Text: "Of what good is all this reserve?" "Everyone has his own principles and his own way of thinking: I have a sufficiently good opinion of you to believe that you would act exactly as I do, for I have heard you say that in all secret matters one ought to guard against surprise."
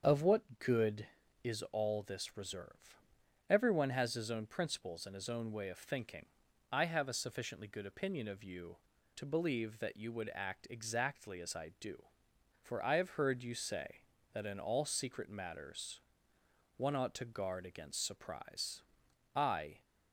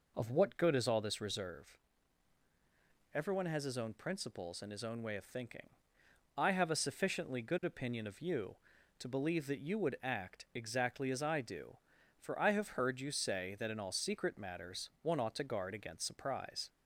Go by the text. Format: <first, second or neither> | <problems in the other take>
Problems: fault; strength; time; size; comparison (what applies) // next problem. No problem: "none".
second | starts louder than the rest; until 1.0 s; 7 dB // pauses between "matters" and "one"; noticeable; at 16.0 s; 0.74 s long // goes on to say "I"; from 19.3 s on; 0.50 s long